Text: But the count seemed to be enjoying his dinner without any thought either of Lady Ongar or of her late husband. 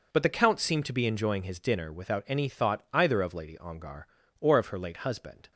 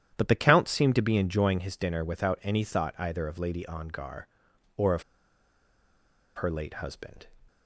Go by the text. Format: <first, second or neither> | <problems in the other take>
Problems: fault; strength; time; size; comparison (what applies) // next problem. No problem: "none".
first | starts louder than the rest; strong; until 1.1 s; 10.5 dB // pauses between "of" and "her"; strong; at 5.0 s; 1.3 s long